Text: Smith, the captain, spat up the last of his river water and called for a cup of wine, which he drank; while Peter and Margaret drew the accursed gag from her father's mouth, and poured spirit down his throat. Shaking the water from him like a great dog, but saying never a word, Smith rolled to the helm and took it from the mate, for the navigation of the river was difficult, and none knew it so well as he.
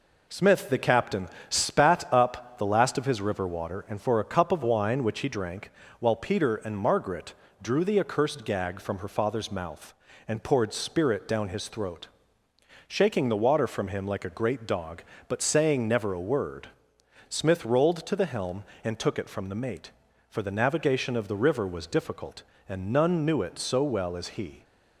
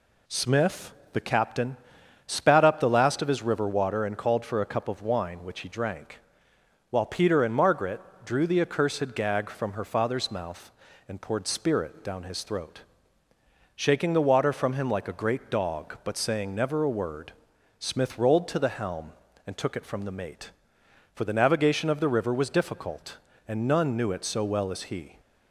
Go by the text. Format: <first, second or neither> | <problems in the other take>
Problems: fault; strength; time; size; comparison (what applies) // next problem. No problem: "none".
second | skips "called"; at 4.0 s // pauses between "Margaret" and "drew"; slight; at 7.3 s; 0.28 s long; slight in the second